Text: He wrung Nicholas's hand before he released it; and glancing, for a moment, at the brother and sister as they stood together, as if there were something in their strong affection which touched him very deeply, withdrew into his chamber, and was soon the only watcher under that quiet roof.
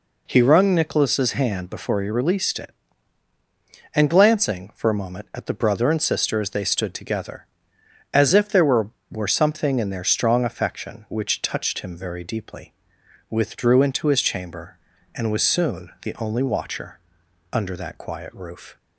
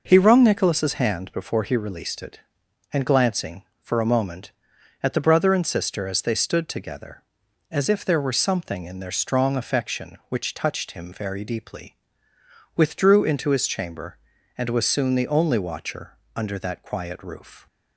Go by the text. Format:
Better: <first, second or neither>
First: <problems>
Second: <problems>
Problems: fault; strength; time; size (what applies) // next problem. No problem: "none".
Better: second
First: says "were" twice; at 9.0 s // pauses between "watcher" and "under"; noticeable; at 16.9 s; 0.54 s long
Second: pauses between "watcher" and "under"; slight; at 16.1 s; 0.24 s long